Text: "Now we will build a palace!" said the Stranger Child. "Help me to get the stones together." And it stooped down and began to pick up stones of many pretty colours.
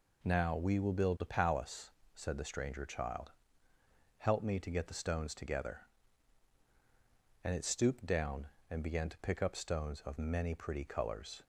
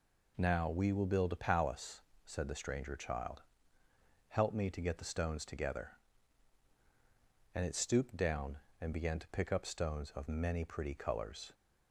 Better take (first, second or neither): neither